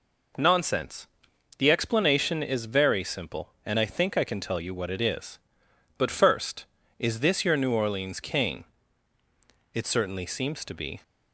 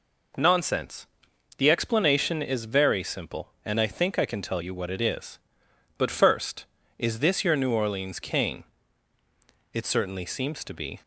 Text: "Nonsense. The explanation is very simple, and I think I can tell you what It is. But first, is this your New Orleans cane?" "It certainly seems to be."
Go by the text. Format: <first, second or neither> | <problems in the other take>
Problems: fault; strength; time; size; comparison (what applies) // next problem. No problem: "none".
neither | none